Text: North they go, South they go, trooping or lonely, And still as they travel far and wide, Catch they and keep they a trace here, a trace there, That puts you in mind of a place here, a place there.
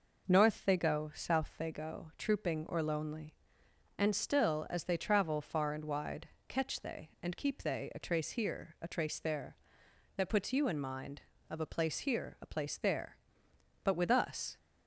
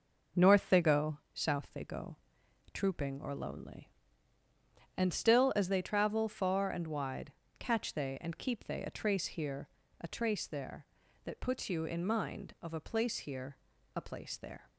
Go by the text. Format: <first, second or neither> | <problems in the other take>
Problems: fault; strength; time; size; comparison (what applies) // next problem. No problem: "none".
second | goes on to say "But with us"; noticeable; from 13.8 s on; 0.74 s long